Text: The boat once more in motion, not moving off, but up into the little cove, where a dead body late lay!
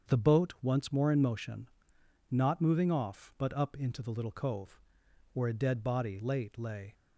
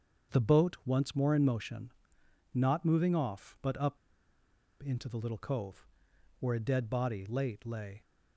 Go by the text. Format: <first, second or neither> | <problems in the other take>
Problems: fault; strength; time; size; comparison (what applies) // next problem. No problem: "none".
first | starts louder than the rest; strong; until 1.4 s; 7 dB; strong in the first // pauses between "up" and "into"; noticeable; at 3.9 s; 0.84 s long